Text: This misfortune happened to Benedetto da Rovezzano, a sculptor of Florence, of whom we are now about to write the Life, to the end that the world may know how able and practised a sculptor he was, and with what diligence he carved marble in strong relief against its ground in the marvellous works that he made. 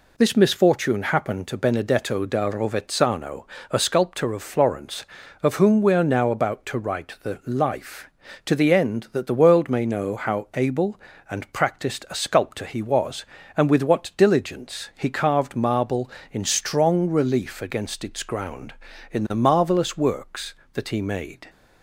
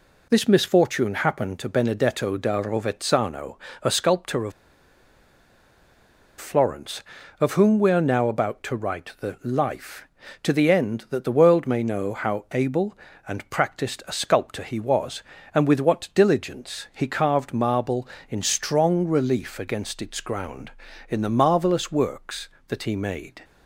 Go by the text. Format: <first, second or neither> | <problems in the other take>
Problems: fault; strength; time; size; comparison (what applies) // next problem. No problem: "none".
first | pauses between "of" and "Florence"; strong; at 4.5 s; 1.8 s long